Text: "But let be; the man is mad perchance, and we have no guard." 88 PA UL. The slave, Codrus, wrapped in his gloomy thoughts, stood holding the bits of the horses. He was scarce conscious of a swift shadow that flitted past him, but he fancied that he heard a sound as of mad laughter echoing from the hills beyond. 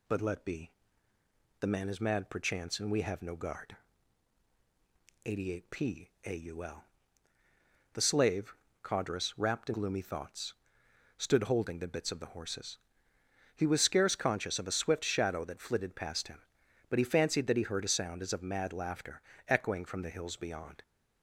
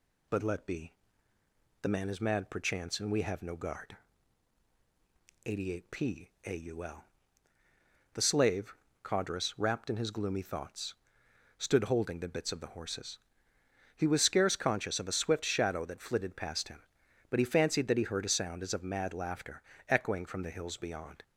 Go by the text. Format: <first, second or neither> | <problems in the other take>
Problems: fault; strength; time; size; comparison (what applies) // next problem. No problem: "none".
second | skips "his"; at 9.7 s // pauses between "laughter" and "echoing"; slight; at 19.2 s; 0.24 s long; slight in the second